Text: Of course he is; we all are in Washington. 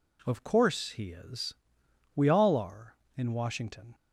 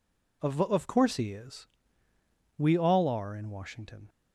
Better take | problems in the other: first | says "Of" twice; at 0.6 s

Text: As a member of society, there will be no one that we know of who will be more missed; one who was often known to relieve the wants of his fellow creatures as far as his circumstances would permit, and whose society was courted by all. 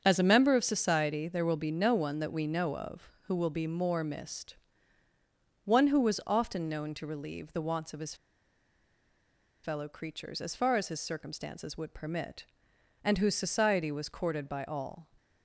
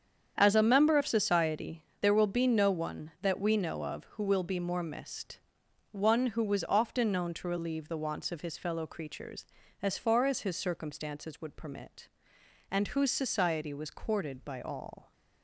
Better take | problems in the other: second | starts louder than the rest; until 1.0 s; 7 dB; strong in the second // pauses between "his" and "fellow"; strong; at 8.1 s; 1.4 s long

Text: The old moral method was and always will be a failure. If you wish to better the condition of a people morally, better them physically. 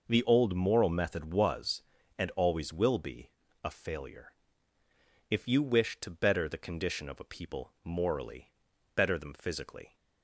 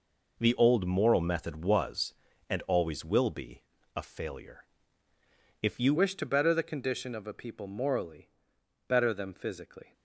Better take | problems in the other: first | pauses between "be" and "a"; slight; at 3.6 s; 0.32 s long; slight in the first // changes voice at "wish"; from 5.9 s on; 4.0 s long

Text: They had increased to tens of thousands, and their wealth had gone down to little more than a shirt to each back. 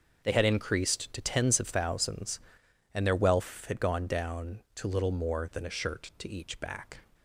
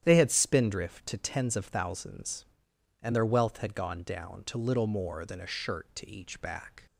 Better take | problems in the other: first | starts louder than the rest; strong; until 1.0 s; 10.5 dB; noticeable in the first // says "spindrift" for "increased"; at 0.2 s

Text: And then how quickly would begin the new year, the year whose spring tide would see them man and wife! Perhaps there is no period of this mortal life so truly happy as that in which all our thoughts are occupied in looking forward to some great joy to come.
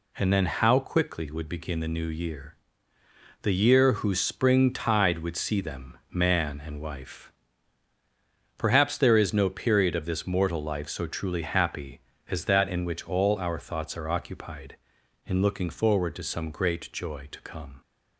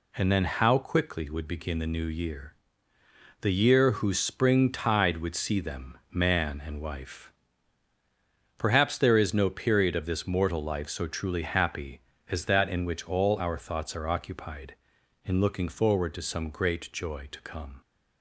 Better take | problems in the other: neither | none

